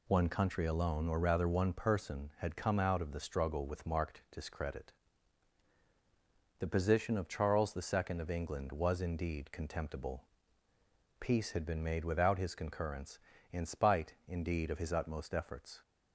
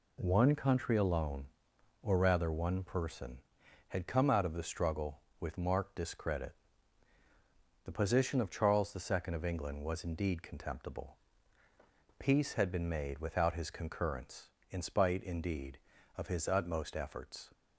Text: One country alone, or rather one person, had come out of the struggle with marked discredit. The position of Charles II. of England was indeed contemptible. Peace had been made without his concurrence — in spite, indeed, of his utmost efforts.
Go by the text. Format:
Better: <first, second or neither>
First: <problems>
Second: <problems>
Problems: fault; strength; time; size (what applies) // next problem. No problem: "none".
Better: neither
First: none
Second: none